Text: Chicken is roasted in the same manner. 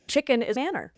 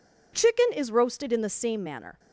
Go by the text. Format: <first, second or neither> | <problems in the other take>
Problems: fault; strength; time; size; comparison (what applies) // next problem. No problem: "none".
second | skips "roasted in the same"; at 0.5 s